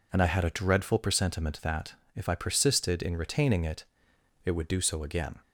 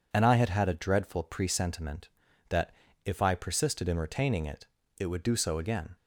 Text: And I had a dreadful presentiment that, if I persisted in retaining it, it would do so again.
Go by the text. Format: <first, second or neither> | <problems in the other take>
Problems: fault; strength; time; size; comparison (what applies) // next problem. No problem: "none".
first | says "had" twice; at 0.4 s